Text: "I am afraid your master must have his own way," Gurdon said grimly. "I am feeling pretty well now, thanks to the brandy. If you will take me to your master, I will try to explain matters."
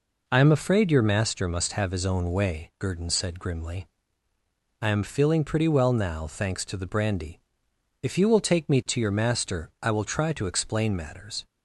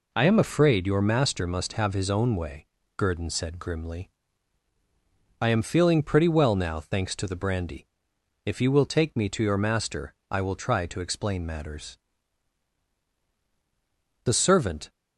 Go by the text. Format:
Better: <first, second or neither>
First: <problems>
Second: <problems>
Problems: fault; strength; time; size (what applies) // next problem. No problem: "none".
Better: first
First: none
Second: goes on to say "The servant"; noticeable; from 14.2 s on; 0.66 s long